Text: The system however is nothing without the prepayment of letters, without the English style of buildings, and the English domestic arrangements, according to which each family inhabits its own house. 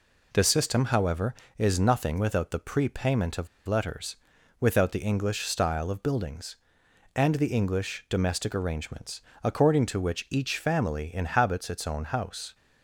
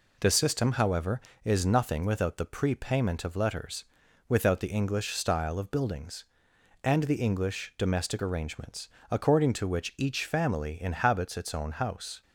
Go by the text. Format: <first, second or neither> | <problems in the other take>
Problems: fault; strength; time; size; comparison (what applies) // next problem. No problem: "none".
second | pauses between "of" and "letters"; slight; at 3.4 s; 0.20 s long